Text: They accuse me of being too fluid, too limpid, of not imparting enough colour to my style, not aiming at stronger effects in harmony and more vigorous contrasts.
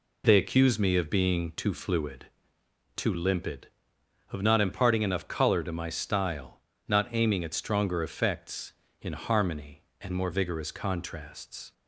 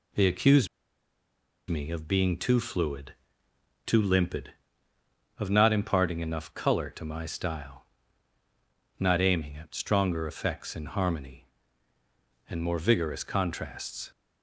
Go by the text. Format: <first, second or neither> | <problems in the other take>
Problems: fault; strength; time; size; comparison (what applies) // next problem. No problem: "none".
first | pauses between "accuse" and "me"; at 0.6 s; 1.0 s long